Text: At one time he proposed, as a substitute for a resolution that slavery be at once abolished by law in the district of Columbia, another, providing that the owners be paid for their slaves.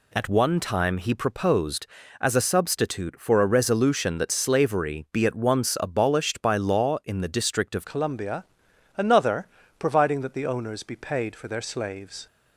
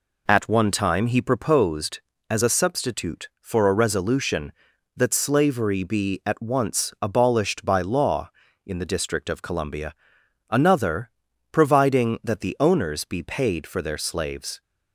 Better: second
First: changes voice at "Columbia"; from 7.8 s on; 4.4 s long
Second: none

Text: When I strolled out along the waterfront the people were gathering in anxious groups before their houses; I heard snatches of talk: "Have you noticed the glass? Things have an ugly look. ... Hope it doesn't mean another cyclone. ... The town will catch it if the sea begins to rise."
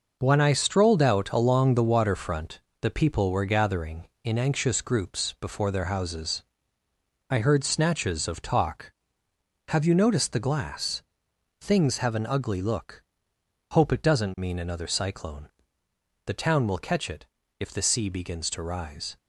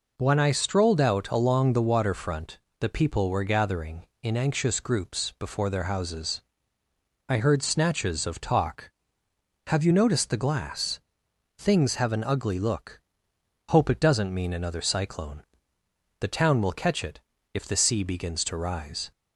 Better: second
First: gets quieter; strong; throughout; 8 dB // pauses between "waterfront" and "the"; slight; at 2.5 s; 0.22 s long // pauses between "it" and "if"; slight; at 17.2 s; 0.34 s long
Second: pauses between "waterfront" and "the"; slight; at 2.5 s; 0.22 s long // pauses between "it" and "if"; slight; at 17.1 s; 0.34 s long

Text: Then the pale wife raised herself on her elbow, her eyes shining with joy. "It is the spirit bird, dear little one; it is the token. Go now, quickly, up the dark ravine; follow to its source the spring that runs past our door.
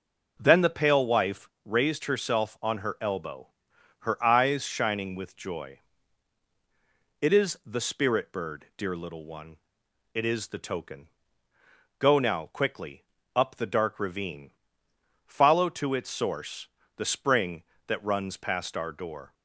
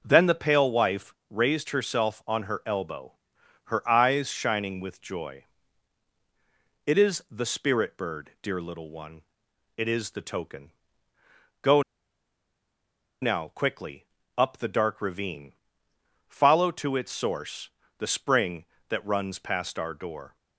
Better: first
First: pauses between "wife" and "raised"; slight; at 1.4 s; 0.16 s long // pauses between "source" and "the"; slight; at 16.6 s; 0.28 s long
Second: pauses between "wife" and "raised"; slight; at 1.1 s; 0.16 s long // pauses between "Go" and "now"; strong; at 11.8 s; 1.3 s long // pauses between "source" and "the"; slight; at 17.6 s; 0.28 s long

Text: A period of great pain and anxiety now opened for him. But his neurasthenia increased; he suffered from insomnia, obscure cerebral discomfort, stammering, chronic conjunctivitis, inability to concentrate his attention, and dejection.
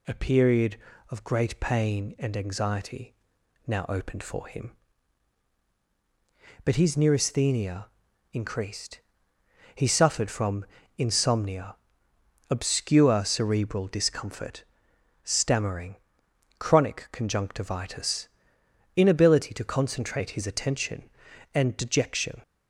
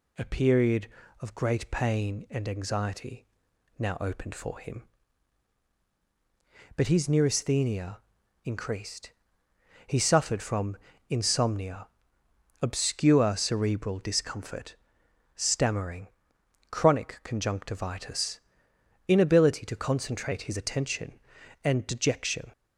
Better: neither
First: pauses between "anxiety" and "now"; noticeable; at 3.1 s; 0.54 s long // pauses between "neurasthenia" and "increased"; noticeable; at 7.8 s; 0.48 s long // pauses between "from" and "insomnia"; slight; at 10.6 s; 0.32 s long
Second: pauses between "anxiety" and "now"; noticeable; at 3.2 s; 0.54 s long // pauses between "neurasthenia" and "increased"; noticeable; at 7.9 s; 0.48 s long // pauses between "from" and "insomnia"; slight; at 10.7 s; 0.32 s long

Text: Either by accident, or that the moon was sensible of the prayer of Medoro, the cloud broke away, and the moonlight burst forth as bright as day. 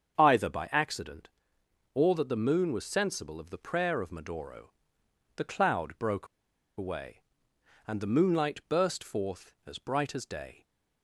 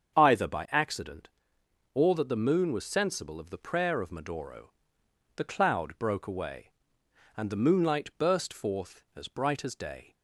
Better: second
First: starts louder than the rest; strong; until 1.2 s; 7.5 dB // pauses between "broke" and "away"; noticeable; at 6.2 s; 0.50 s long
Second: starts louder than the rest; strong; until 1.2 s; 7.5 dB

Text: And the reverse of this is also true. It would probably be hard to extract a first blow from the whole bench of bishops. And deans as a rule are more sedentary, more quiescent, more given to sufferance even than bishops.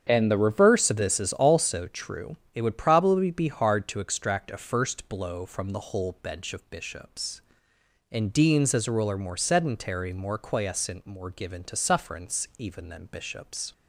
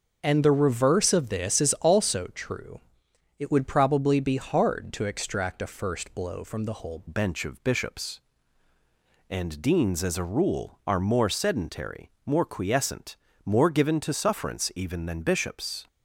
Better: first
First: starts louder than the rest; strong; until 1.1 s; 8 dB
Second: starts louder than the rest; until 1.2 s; 6.5 dB // changes voice at "bench"; from 7.0 s on; 8.8 s long

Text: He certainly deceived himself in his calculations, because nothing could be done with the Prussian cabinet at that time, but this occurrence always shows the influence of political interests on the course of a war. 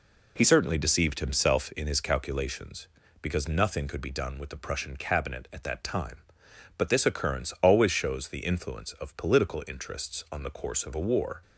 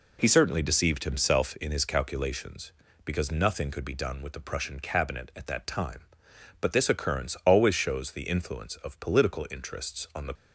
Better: first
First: none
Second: stops before "course of a war"; at 10.3 s

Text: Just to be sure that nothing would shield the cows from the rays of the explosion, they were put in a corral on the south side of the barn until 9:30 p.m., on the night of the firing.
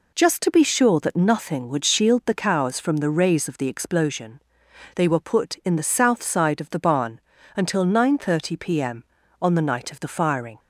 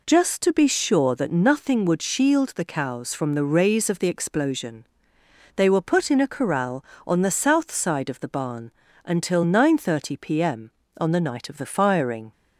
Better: second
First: skips "a corral on"; at 5.7 s // pauses between "barn" and "until"; slight; at 7.2 s; 0.34 s long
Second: pauses between "barn" and "until"; slight; at 8.7 s; 0.34 s long

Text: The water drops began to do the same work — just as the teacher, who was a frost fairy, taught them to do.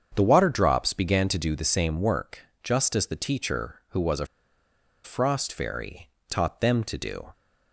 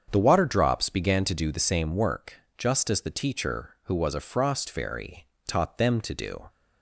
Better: second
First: starts louder than the rest; strong; until 1.1 s; 7.5 dB // pauses between "a" and "frost"; noticeable; at 4.2 s; 0.77 s long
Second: starts louder than the rest; strong; until 1.1 s; 7.5 dB

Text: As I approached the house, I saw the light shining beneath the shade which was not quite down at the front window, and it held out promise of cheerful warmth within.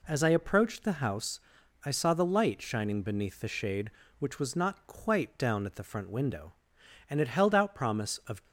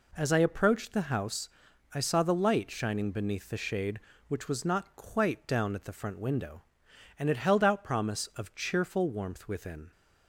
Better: second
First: stops before "cheerful warmth within"; at 8.4 s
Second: none

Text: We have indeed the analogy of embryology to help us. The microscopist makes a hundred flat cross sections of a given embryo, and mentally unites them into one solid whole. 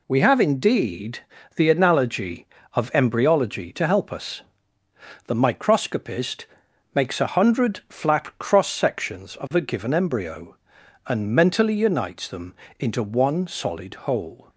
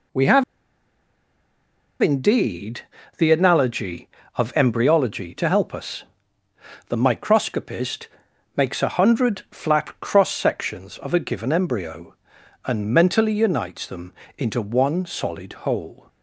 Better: first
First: pauses between "indeed" and "the"; slight; at 1.1 s; 0.36 s long // pauses between "microscopist" and "makes"; noticeable; at 6.4 s; 0.50 s long // pauses between "them" and "into"; slight; at 12.5 s; 0.26 s long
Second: pauses between "have" and "indeed"; strong; at 0.4 s; 1.5 s long // pauses between "indeed" and "the"; slight; at 2.8 s; 0.36 s long // pauses between "microscopist" and "makes"; noticeable; at 8.0 s; 0.50 s long // pauses between "them" and "into"; slight; at 14.1 s; 0.26 s long

